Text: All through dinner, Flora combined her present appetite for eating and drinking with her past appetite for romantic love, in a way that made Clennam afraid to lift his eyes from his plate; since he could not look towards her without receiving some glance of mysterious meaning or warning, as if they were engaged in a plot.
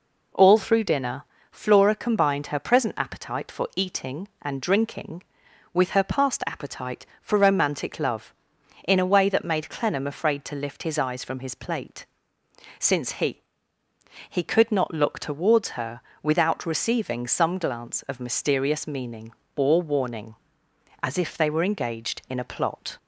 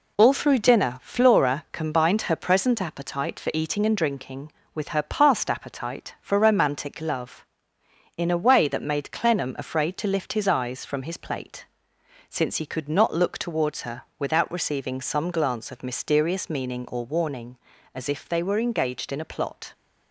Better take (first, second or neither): second